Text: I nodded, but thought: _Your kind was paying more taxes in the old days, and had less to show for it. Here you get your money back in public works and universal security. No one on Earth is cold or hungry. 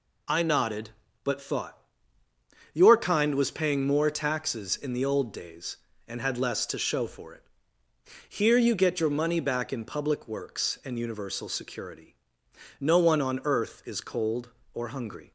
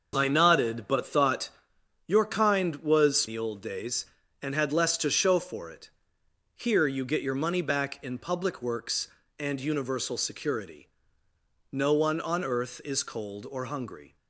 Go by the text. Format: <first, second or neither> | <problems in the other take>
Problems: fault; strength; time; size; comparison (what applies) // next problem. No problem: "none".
first | starts louder than the rest; noticeable; until 1.1 s; 6 dB // skips "paying more taxes in"; at 3.2 s